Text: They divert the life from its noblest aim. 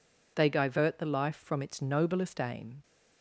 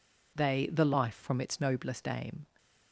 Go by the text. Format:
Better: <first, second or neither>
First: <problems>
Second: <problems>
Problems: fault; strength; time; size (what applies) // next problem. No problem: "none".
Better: first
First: none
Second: skips "divert"; at 0.6 s